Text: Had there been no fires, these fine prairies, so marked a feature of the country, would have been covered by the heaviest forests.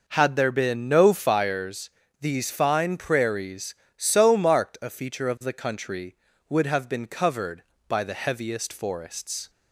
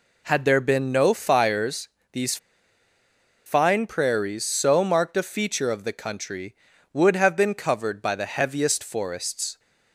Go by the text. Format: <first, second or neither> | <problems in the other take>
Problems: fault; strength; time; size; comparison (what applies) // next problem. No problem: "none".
first | pauses between "these" and "fine"; at 2.3 s; 1.0 s long